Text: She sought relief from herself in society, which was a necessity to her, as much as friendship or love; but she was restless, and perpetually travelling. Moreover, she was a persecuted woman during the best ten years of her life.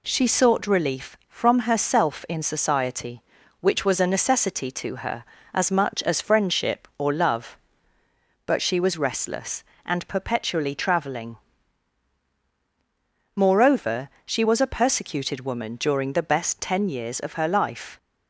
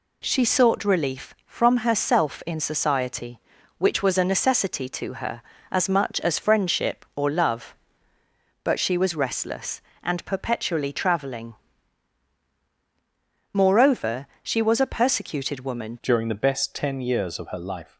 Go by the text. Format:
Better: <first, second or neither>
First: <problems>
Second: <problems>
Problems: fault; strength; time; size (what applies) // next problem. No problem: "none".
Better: first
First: none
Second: changes voice at "during"; from 16.0 s on; 1.9 s long